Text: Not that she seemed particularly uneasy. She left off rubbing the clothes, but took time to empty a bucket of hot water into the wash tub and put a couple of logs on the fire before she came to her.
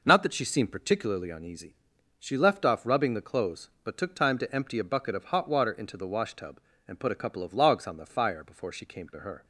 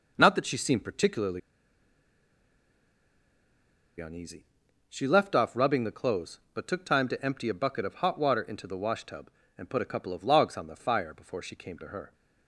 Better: first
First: none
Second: pauses between "particularly" and "uneasy"; strong; at 1.4 s; 2.6 s long

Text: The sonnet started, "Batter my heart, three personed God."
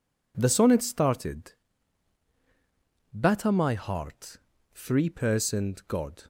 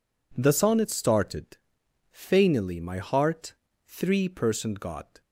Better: first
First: none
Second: says "Fainily" for "Batter"; at 2.1 s

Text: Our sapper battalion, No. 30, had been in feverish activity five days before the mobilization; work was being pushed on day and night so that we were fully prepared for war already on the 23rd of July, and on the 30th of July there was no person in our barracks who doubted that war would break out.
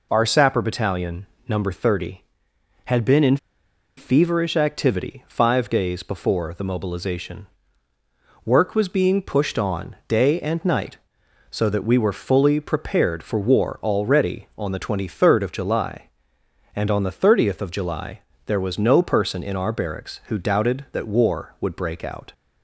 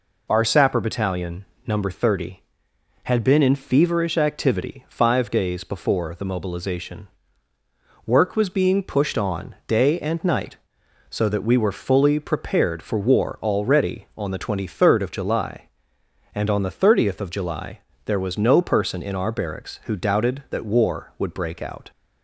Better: second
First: pauses between "in" and "feverish"; noticeable; at 3.3 s; 0.60 s long // pauses between "July" and "there"; slight; at 18.1 s; 0.28 s long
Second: pauses between "July" and "there"; slight; at 17.7 s; 0.28 s long

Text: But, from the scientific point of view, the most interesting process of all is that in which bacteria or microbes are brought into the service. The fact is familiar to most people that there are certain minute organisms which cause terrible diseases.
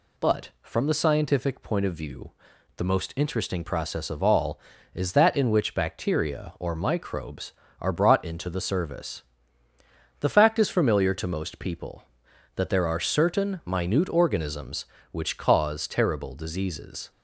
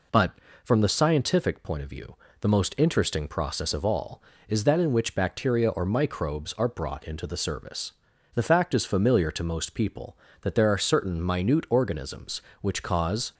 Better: first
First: none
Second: stops before "terrible diseases"; at 13.3 s

